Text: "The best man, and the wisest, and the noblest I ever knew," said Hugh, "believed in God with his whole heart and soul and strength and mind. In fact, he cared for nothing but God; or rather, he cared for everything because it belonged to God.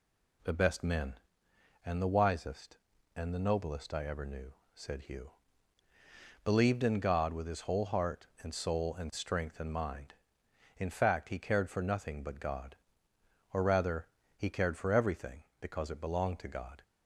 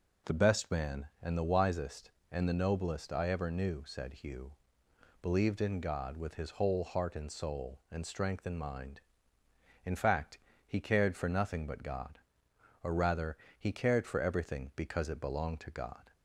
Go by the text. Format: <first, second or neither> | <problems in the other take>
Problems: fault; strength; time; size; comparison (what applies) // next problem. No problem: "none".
second | says "men" for "man"; at 0.8 s